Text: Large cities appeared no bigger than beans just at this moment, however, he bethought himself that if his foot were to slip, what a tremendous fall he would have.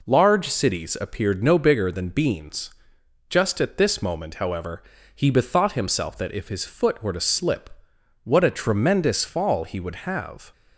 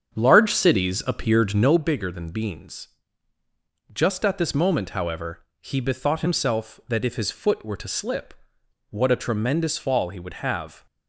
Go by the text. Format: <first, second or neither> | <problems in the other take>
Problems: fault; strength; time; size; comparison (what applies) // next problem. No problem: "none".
first | starts louder than the rest; strong; until 1.8 s; 7 dB // pauses between "beans" and "just"; at 2.8 s; 1.0 s long; noticeable in the first